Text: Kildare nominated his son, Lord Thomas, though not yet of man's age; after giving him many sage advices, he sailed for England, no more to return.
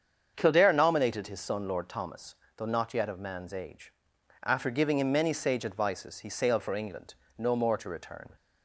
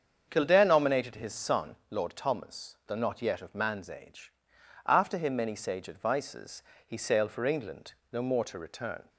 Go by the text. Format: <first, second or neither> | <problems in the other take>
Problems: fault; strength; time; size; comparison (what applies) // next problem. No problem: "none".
first | starts louder than the rest; strong; until 1.2 s; 7 dB; strong in the first // skips "giving"; at 5.1 s